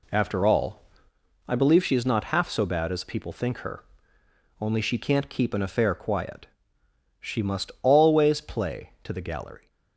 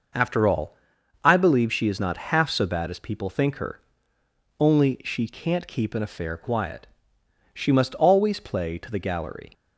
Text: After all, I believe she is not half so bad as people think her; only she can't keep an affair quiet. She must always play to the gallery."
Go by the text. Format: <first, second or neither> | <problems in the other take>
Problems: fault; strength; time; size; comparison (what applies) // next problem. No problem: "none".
neither | none